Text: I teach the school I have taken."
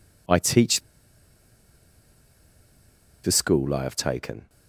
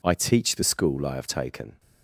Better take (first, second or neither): second